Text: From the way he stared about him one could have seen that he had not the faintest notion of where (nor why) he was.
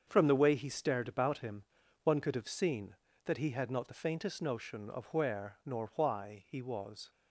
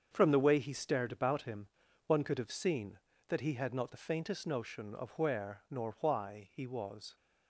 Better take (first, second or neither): neither